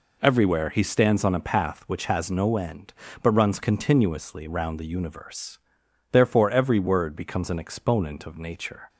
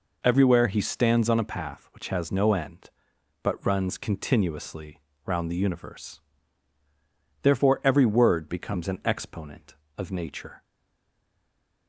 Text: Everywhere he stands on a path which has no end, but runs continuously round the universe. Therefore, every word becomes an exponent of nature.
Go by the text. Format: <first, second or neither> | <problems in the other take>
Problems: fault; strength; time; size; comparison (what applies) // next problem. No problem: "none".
first | pauses between "continuously" and "round"; slight; at 4.9 s; 0.26 s long // stays silent after the last word; noticeable; from 10.6 s on; 1.2 s long